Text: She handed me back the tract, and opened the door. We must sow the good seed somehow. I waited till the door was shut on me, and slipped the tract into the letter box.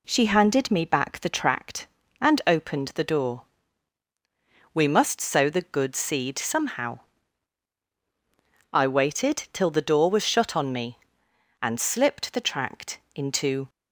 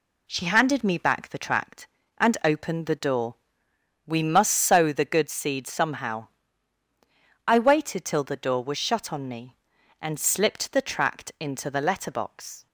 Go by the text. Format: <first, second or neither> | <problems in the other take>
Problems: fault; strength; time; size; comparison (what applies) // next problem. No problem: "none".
second | pauses between "tract" and "into"; slight; at 12.9 s; 0.16 s long // stops before "the letter box"; at 13.6 s